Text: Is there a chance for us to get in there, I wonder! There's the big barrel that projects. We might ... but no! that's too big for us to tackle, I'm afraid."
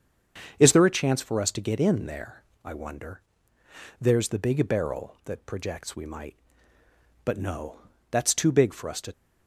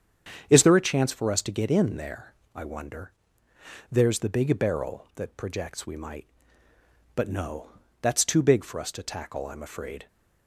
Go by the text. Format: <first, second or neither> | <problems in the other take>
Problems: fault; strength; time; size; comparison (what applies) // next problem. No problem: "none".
second | starts louder than the rest; until 1.6 s; 7 dB; strong in the second // stops before "tackle I'm afraid"; at 9.1 s